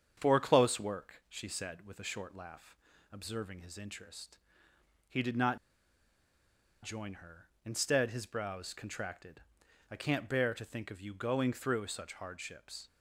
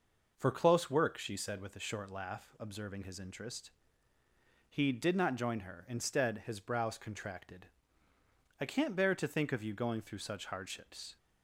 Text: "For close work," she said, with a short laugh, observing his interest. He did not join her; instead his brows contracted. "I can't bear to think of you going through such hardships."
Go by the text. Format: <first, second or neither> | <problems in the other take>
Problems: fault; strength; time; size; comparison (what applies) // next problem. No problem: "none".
second | starts louder than the rest; strong; until 1.2 s; 7.5 dB // pauses between "not" and "join"; strong; at 5.5 s; 1.2 s long